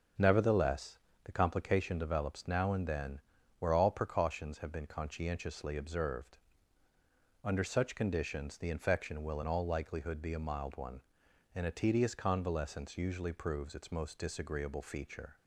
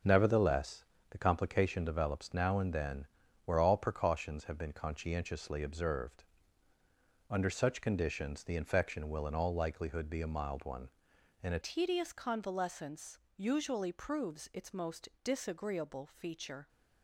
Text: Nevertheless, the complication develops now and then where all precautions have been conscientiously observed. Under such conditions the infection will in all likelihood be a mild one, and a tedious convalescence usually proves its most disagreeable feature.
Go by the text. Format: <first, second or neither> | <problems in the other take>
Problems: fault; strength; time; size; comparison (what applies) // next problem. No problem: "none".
first | starts louder than the rest; until 1.3 s; 7 dB; also in the first // pauses between "then" and "where"; at 3.0 s; 0.40 s long; also in the first // changes voice at "tedious"; from 11.6 s on; 5.0 s long // pauses between "convalescence" and "usually"; slight; at 13.1 s; 0.20 s long // pauses between "most" and "disagreeable"; slight; at 15.0 s; 0.16 s long